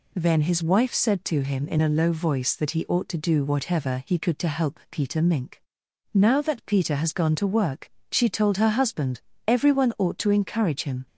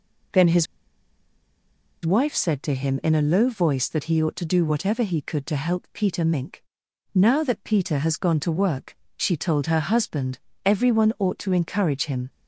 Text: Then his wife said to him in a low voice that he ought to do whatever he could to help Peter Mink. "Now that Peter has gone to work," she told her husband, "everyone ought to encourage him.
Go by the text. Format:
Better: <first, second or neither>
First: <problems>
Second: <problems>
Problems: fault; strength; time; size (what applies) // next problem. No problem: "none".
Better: first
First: none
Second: pauses between "his" and "wife"; strong; at 0.6 s; 1.4 s long